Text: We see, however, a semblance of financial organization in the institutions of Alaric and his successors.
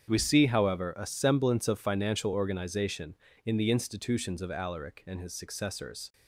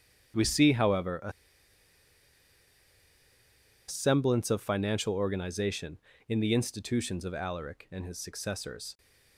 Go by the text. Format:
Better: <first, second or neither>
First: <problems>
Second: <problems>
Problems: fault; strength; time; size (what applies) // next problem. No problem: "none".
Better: first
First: starts louder than the rest; strong; until 1.1 s; 8 dB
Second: starts louder than the rest; strong; until 3.9 s; 8 dB // pauses between "a" and "semblance"; strong; at 1.3 s; 2.5 s long